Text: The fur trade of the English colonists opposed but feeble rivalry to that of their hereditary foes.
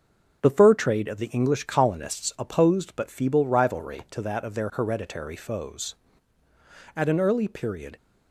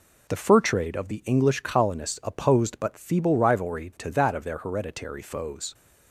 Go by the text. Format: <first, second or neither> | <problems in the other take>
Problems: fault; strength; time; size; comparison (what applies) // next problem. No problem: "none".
second | starts louder than the rest; until 1.4 s; 6.5 dB // goes on to say "At an early period"; noticeable; from 6.9 s on; 1.0 s long